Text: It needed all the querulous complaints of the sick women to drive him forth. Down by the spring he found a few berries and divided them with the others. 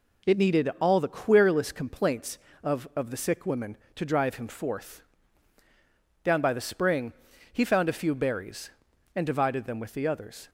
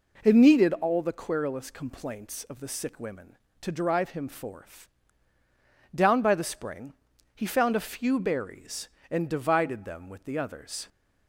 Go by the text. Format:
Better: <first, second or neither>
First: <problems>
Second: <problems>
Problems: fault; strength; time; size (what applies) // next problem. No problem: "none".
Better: second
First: says "of" twice; at 2.9 s // pauses between "spring" and "he"; at 7.1 s; 0.38 s long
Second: pauses between "spring" and "he"; at 6.9 s; 0.42 s long